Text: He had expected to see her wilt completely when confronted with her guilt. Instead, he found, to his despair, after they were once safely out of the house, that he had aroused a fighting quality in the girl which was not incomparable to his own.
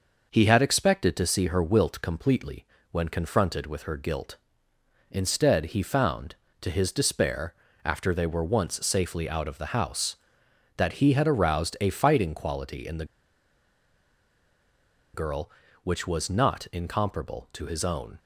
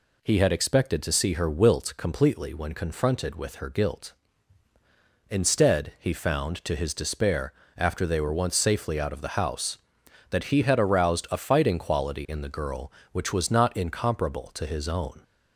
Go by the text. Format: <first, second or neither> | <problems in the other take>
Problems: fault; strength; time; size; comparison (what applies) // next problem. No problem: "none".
second | pauses between "completely" and "when"; slight; at 2.6 s; 0.26 s long // pauses between "the" and "girl"; strong; at 13.0 s; 2.0 s long